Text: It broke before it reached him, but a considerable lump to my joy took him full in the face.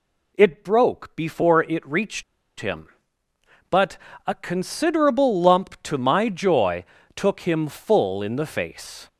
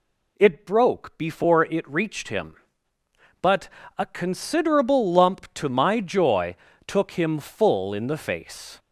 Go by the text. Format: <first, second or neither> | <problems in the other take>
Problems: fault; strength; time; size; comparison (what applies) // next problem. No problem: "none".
second | pauses between "reached" and "him"; at 2.2 s; 0.36 s long // pauses between "but" and "a"; slight; at 3.9 s; 0.30 s long; slight in the second // pauses between "joy" and "took"; slight; at 6.8 s; 0.32 s long; slight in the second